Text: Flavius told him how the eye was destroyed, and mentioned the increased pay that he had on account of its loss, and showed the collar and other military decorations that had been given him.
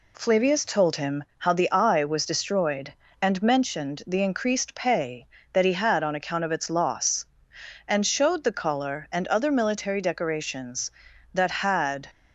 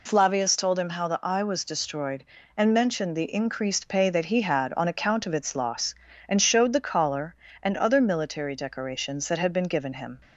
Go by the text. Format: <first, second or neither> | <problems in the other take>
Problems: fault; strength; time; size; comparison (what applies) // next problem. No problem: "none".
second | stops before "been given him"; at 12.0 s